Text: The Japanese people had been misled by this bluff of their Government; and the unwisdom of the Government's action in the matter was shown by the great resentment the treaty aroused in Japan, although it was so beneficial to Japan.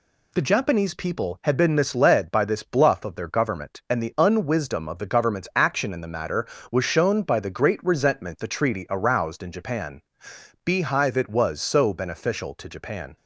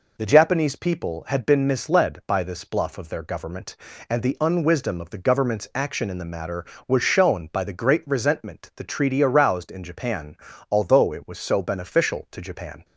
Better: second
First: says "beehive" for "although"; at 10.6 s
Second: none

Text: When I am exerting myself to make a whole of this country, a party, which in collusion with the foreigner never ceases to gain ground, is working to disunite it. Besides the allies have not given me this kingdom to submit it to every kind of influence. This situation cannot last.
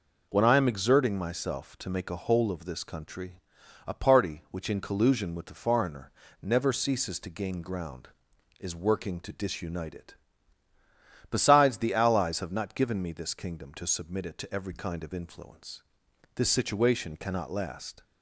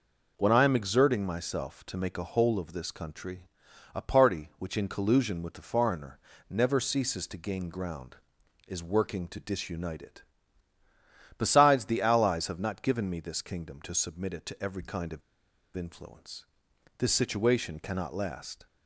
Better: first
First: pauses between "foreigner" and "never"; slight; at 6.0 s; 0.32 s long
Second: pauses between "foreigner" and "never"; slight; at 6.1 s; 0.32 s long // pauses between "of" and "influence"; noticeable; at 15.2 s; 0.55 s long

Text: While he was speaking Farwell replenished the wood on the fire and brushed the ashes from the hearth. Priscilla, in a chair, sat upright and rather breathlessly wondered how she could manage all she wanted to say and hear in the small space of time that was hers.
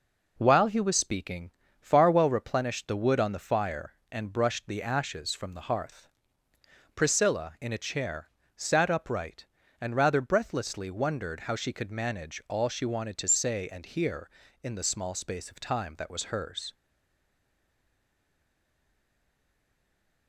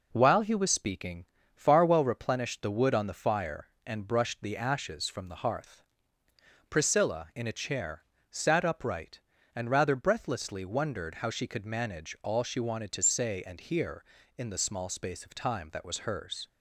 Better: second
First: pauses between "speaking" and "Farwell"; slight; at 1.4 s; 0.32 s long // stays silent after the last word; strong; from 16.7 s on; 3.5 s long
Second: pauses between "speaking" and "Farwell"; slight; at 1.2 s; 0.32 s long

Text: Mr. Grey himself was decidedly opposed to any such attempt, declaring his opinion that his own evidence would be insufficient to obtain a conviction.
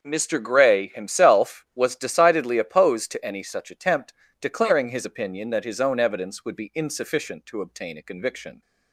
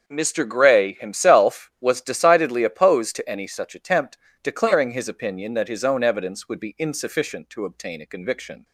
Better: neither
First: starts louder than the rest; until 1.0 s; 7 dB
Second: starts louder than the rest; until 1.0 s; 7 dB

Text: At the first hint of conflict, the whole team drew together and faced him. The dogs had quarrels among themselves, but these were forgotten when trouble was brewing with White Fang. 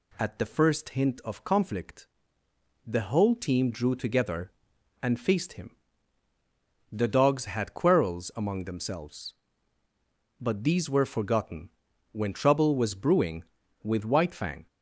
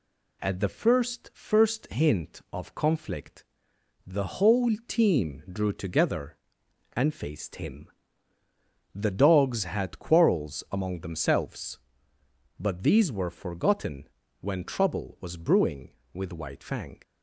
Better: first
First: pauses between "forgotten" and "when"; at 11.7 s; 0.42 s long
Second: says "first" twice; at 1.3 s // pauses between "forgotten" and "when"; slight; at 14.0 s; 0.34 s long

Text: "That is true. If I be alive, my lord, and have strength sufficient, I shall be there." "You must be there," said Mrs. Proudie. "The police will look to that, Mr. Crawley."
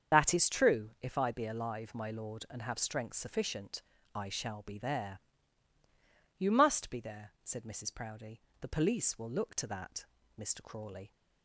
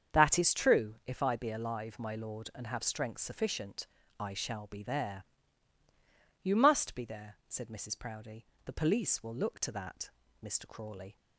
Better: second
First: loses the start of "That"; at 0.1 s; 40 ms // starts louder than the rest; strong; until 1.2 s; 7.5 dB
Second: starts louder than the rest; strong; until 1.2 s; 7 dB

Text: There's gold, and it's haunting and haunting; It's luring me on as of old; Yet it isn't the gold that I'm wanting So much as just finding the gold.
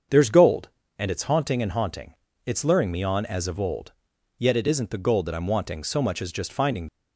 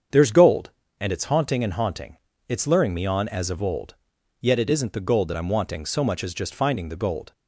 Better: second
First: starts louder than the rest; until 1.3 s; 7 dB // stops before "the gold"; at 6.8 s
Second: starts louder than the rest; strong; until 1.4 s; 7.5 dB

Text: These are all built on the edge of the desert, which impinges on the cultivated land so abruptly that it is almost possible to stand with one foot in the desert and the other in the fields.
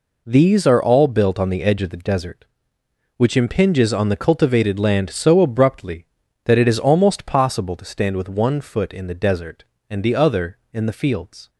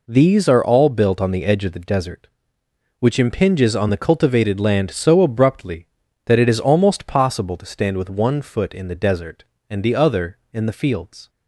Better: neither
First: none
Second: none

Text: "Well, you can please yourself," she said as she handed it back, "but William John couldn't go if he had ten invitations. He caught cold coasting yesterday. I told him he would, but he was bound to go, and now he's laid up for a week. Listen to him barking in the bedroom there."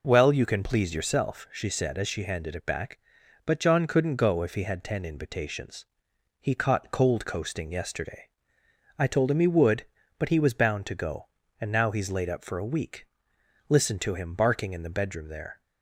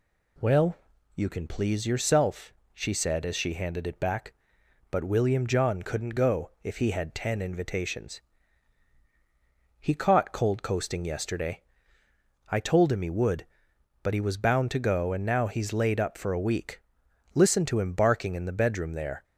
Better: second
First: skips "William"; at 3.5 s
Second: none

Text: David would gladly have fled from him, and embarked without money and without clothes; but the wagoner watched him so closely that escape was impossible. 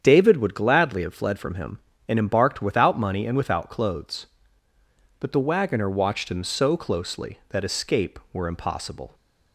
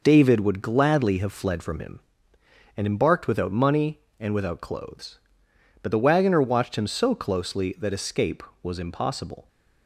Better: second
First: starts louder than the rest; strong; until 1.0 s; 8 dB // says "were" for "was"; at 8.3 s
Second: none

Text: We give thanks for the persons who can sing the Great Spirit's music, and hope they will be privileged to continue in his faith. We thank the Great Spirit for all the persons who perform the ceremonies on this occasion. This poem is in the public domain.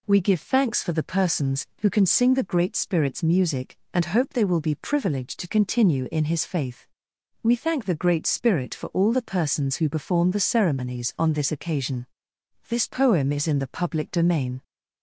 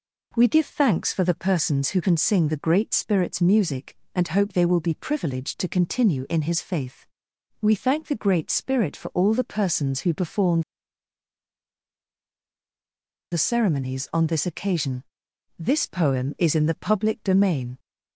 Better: first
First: none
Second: pauses between "perform" and "the"; strong; at 10.6 s; 2.6 s long

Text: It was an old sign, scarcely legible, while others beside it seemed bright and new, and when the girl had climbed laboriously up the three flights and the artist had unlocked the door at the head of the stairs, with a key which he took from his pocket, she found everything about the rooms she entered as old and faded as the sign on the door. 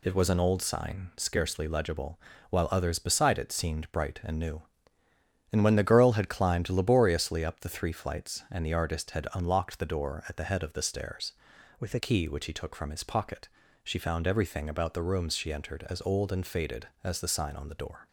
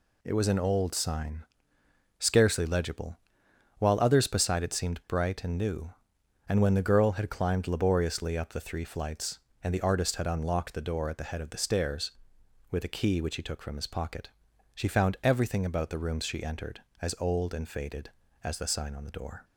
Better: second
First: changes voice from "with" to "a"; from 11.7 to 11.9 s; 0.2 s long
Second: none

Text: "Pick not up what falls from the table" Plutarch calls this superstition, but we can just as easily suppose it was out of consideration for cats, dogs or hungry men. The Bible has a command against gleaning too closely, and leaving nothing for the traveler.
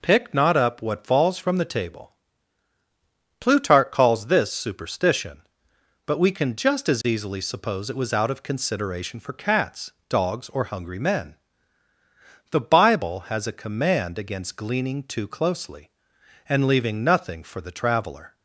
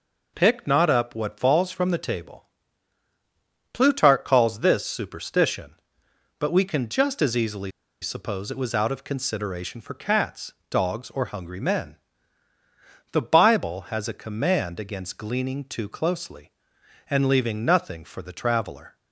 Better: first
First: pauses between "table" and "Plutarch"; at 2.1 s; 1.2 s long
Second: pauses between "table" and "Plutarch"; at 2.4 s; 1.2 s long // pauses between "easily" and "suppose"; slight; at 7.7 s; 0.31 s long

